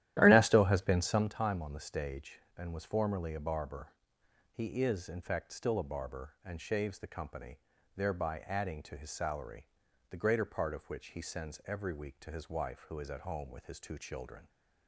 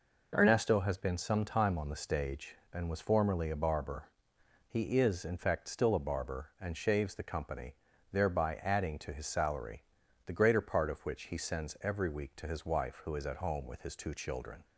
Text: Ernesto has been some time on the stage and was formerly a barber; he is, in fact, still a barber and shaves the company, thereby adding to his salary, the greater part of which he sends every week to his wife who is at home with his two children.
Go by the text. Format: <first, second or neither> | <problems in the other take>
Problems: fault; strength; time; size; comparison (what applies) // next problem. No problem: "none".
second | starts louder than the rest; strong; until 1.3 s; 13 dB